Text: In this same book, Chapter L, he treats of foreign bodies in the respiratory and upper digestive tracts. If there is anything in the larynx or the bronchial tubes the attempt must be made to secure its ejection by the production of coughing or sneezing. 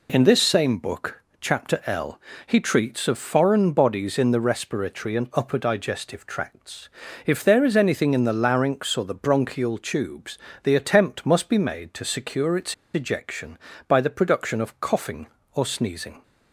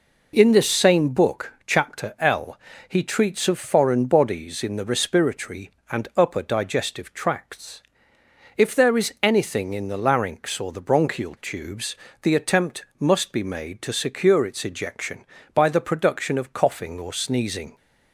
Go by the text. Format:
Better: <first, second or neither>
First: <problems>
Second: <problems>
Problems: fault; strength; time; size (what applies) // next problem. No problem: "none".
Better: second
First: pauses between "tubes" and "the"; slight; at 10.3 s; 0.28 s long // pauses between "its" and "ejection"; slight; at 12.7 s; 0.19 s long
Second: pauses between "tubes" and "the"; slight; at 11.9 s; 0.26 s long